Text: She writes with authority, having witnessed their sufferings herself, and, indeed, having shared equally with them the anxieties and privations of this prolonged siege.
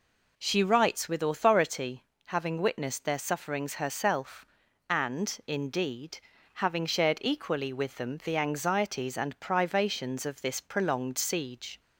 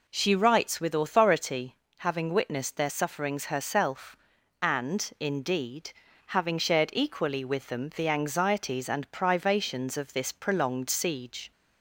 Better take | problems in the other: neither | none

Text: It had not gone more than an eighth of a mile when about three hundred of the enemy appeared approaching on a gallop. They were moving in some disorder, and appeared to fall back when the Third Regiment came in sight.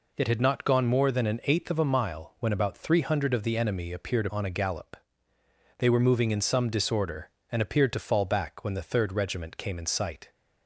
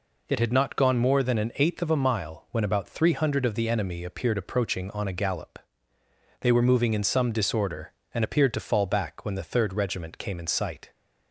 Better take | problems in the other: second | skips "approaching"; at 4.2 s

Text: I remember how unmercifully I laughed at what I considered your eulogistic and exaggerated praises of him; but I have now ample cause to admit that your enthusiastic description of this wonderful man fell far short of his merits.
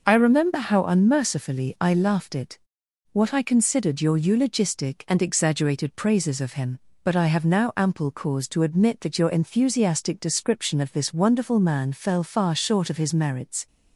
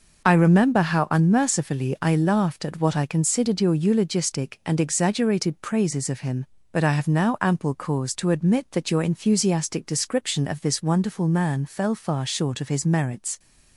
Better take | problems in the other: second | says "it" for "at"; at 2.3 s

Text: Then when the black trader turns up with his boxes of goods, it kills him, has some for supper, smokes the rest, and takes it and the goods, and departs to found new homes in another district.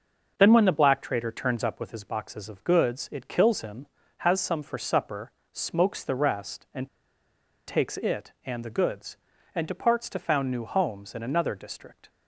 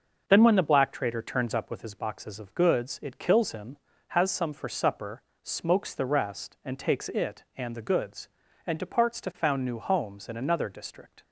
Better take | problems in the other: second | pauses between "and" and "takes"; noticeable; at 6.8 s; 0.79 s long

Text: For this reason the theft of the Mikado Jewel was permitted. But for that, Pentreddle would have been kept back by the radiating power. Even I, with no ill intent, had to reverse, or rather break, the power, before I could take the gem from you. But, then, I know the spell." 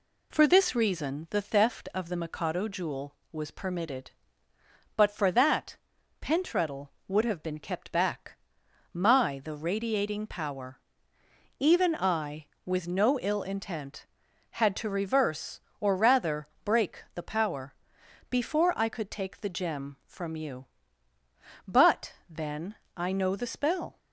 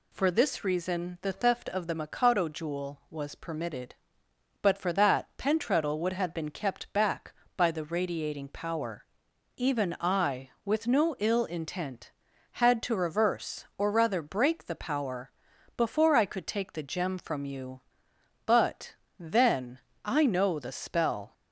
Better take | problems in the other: second | says "my" for "by"; at 8.9 s // pauses between "rather" and "break"; slight; at 16.4 s; 0.16 s long

